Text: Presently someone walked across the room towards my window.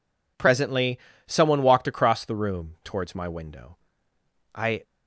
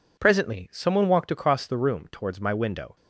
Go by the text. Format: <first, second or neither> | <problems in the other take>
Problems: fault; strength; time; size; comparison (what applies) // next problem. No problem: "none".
second | pauses between "Presently" and "someone"; slight; at 0.9 s; 0.28 s long // goes on to say "I"; slight; from 4.5 s on; 0.30 s long